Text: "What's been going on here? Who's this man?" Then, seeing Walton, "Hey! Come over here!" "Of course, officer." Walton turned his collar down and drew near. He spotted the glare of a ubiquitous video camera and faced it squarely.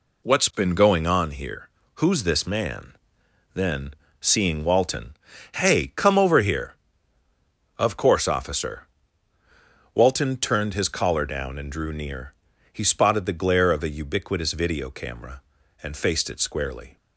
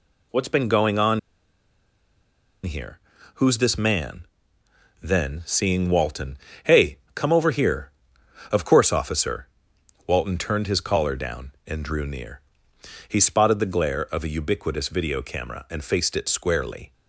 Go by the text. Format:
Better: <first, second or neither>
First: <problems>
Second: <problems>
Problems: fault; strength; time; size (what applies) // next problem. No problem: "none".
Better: first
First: none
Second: pauses between "on" and "here"; strong; at 1.1 s; 1.4 s long